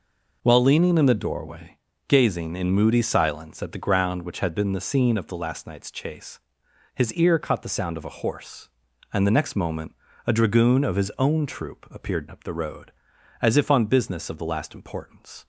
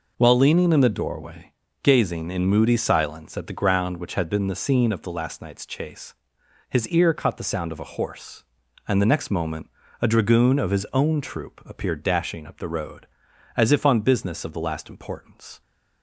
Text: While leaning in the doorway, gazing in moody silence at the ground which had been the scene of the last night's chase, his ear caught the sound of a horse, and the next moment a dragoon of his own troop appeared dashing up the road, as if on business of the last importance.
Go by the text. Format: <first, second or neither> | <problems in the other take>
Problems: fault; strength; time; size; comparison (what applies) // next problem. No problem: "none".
second | pauses between "moment" and "a"; slight; at 9.9 s; 0.32 s long; slight in the second // skips "dashing"; at 12.2 s